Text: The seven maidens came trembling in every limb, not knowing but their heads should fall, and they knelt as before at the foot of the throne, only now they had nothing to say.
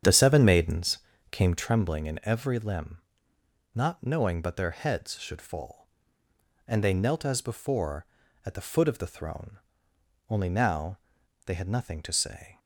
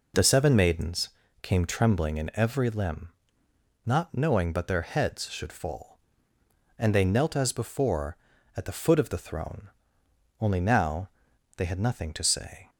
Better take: second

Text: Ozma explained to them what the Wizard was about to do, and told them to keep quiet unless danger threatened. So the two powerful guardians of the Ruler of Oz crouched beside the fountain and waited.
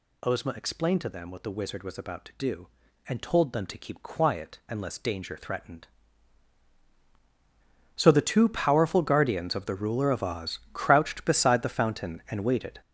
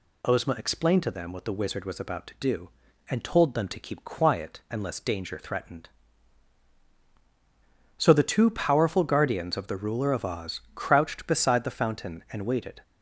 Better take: second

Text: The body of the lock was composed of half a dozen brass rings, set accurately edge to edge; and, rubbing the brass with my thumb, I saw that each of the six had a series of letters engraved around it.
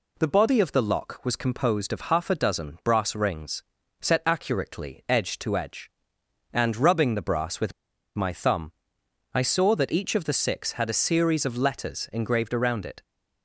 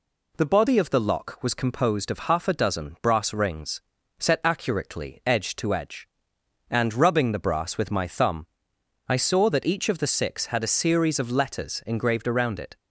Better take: second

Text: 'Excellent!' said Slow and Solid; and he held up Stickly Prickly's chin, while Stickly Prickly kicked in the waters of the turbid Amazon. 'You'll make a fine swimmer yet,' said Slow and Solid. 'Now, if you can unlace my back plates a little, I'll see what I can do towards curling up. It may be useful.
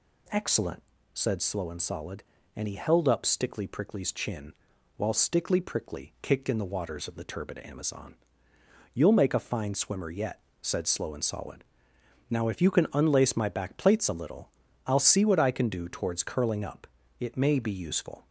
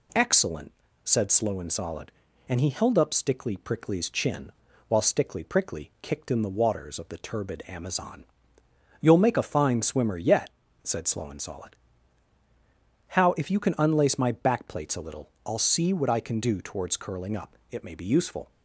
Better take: first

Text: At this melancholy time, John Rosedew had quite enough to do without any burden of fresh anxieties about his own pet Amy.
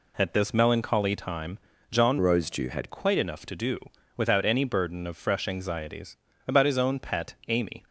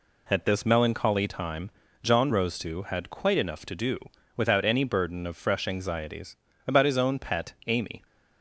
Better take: second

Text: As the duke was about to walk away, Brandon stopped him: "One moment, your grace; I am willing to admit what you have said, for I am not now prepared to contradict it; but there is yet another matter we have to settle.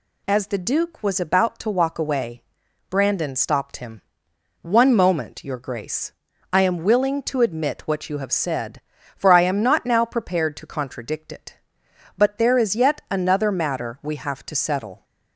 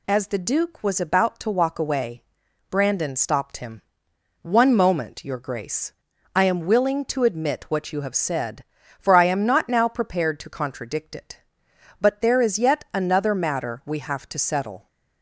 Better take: neither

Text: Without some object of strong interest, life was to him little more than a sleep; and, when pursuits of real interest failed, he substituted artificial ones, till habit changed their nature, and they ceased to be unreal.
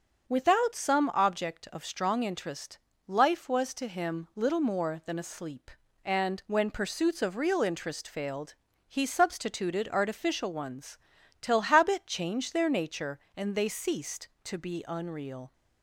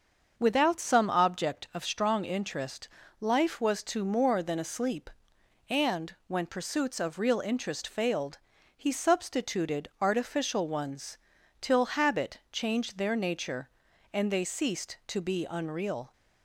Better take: first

